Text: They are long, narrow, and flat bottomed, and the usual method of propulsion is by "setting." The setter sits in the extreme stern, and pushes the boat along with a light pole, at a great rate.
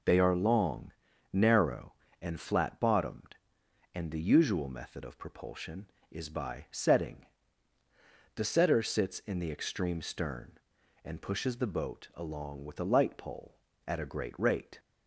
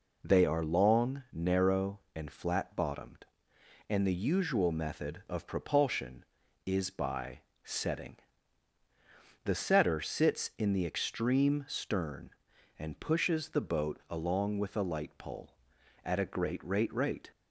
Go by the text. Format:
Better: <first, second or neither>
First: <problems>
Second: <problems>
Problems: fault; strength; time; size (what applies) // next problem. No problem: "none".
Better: first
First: none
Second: pauses between "by" and "setting"; slight; at 7.4 s; 0.20 s long // says "rate" twice; at 16.9 s